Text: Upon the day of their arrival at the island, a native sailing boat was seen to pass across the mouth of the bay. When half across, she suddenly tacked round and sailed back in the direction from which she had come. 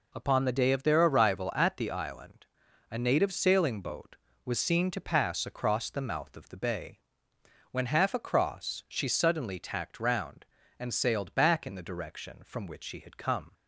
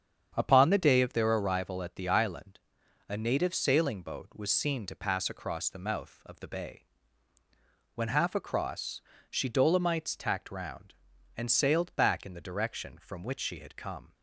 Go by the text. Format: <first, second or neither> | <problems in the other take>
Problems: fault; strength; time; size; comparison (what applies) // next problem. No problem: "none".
first | starts louder than the rest; strong; until 1.3 s; 8 dB // says "dolomites" for "suddenly"; at 9.4 s